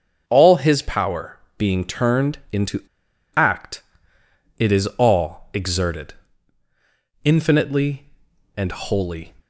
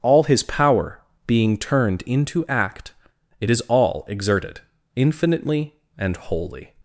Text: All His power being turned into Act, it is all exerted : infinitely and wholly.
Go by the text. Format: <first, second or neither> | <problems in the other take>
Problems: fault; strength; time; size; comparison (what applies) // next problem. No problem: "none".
second | starts louder than the rest; until 1.2 s; 6.5 dB; also in the second // pauses between "power" and "being"; slight; at 1.3 s; 0.18 s long; slight in the second // pauses between "into" and "Act"; noticeable; at 2.8 s; 0.53 s long